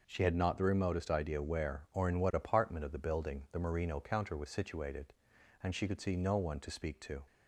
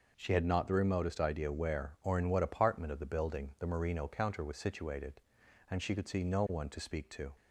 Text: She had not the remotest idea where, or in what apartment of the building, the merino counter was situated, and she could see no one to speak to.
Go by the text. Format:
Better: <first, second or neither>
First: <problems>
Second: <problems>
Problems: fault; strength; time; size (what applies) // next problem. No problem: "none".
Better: neither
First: none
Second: none